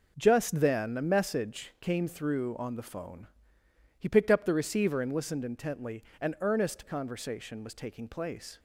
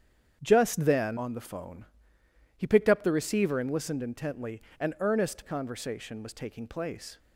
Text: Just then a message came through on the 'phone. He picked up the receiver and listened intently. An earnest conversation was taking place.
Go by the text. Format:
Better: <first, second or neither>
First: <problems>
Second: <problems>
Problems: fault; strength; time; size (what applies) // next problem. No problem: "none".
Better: first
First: none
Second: starts louder than the rest; strong; until 1.4 s; 8.5 dB // skips "a message came through"; at 1.1 s